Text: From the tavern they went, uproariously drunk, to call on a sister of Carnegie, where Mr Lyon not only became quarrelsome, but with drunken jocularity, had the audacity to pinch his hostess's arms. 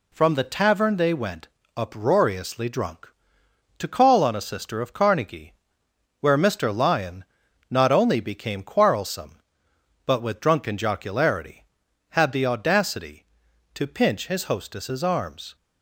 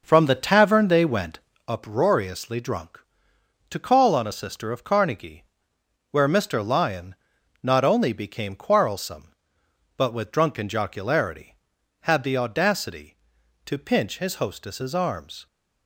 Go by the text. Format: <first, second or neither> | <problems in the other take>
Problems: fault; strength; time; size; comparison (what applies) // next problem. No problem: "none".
first | starts louder than the rest; noticeable; until 1.8 s; 6 dB // pauses between "Lyon" and "not"; noticeable; at 7.1 s; 0.46 s long; also in the first